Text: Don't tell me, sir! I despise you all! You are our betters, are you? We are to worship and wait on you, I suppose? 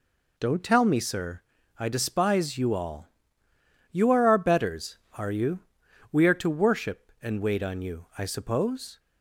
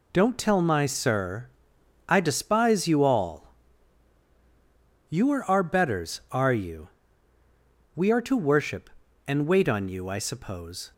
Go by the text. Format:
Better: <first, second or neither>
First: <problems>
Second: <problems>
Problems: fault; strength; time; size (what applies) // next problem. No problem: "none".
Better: first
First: none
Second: says "my" for "me"; at 0.5 s